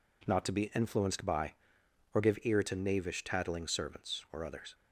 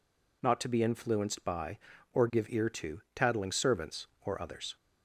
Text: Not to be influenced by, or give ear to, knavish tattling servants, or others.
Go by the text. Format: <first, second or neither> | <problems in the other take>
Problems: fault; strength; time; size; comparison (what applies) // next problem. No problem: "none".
first | skips "knavish"; at 3.0 s